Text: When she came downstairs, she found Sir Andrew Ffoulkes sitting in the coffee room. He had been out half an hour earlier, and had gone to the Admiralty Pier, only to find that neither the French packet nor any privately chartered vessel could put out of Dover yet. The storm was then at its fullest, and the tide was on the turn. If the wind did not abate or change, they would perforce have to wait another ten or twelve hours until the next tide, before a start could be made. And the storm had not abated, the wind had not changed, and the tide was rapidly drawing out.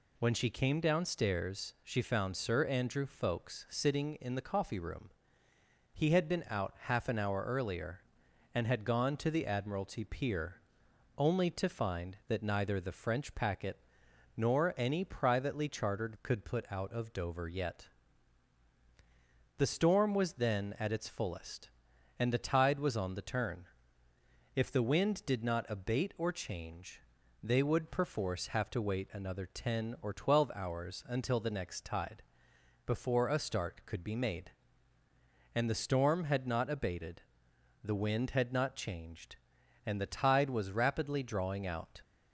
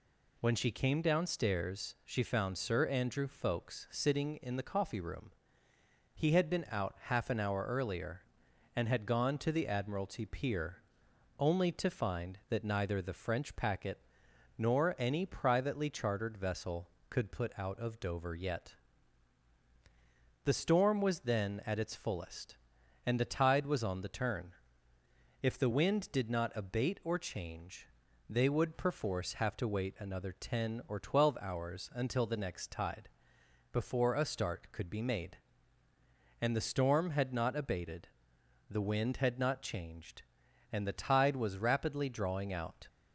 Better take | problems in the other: second | pauses between "packet" and "nor"; noticeable; at 13.7 s; 0.60 s long; noticeable in the second // skips "vessel"; at 16.1 s

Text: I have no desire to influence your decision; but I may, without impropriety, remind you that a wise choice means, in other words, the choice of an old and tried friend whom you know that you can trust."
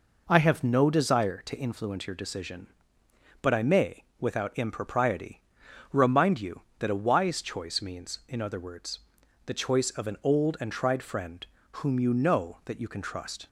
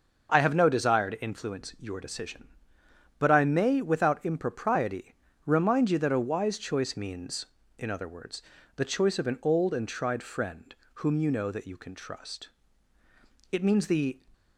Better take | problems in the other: first | starts louder than the rest; until 1.3 s; 6.5 dB // pauses between "friend" and "whom"; slight; at 10.7 s; 0.22 s long; slight in the first // goes on to say "It means the"; noticeable; from 13.5 s on; 0.70 s long

